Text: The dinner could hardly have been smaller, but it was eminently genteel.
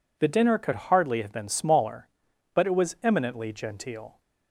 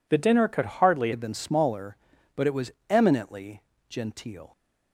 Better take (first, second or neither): first